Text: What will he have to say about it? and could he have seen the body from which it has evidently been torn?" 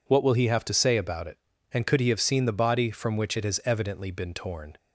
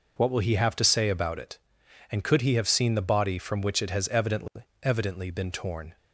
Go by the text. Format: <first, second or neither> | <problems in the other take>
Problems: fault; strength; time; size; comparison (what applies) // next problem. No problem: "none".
first | says "evidently" twice; at 4.8 s